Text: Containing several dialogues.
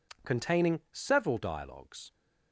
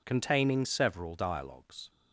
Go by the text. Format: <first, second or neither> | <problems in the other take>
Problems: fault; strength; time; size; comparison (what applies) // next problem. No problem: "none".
neither | none